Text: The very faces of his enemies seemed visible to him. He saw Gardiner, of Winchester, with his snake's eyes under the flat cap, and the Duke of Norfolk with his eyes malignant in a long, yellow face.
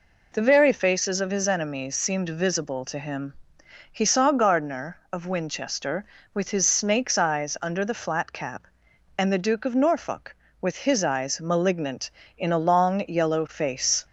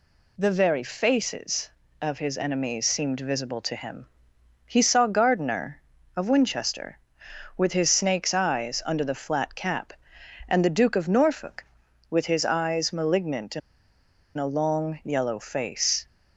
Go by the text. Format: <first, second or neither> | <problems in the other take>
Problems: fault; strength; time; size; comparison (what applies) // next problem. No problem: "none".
first | pauses between "in" and "a"; noticeable; at 13.6 s; 0.77 s long